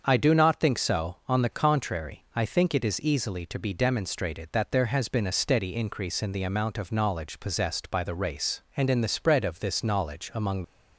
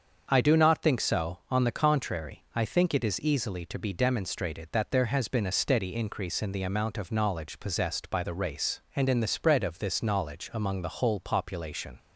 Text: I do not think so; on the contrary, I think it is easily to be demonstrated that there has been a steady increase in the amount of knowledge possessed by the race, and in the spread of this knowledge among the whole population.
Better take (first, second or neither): second